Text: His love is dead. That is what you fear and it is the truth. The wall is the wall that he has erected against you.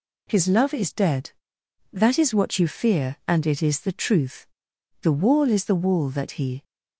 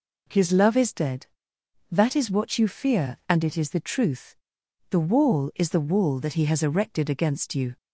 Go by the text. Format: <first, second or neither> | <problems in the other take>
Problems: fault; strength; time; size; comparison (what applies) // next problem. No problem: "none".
second | stops before "has erected against you"; at 6.6 s